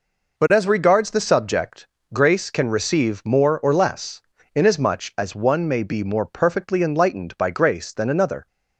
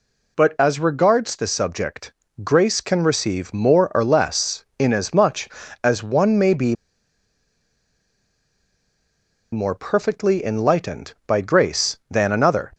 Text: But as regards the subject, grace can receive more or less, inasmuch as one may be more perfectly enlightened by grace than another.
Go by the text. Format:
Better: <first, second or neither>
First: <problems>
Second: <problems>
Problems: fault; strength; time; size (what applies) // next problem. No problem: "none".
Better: first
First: none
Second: pauses between "be" and "more"; strong; at 6.7 s; 2.7 s long